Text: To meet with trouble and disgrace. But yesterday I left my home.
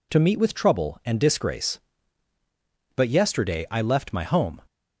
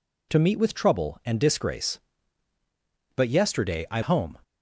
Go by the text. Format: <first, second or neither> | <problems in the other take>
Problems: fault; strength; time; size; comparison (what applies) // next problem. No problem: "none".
first | skips "left my"; at 4.0 s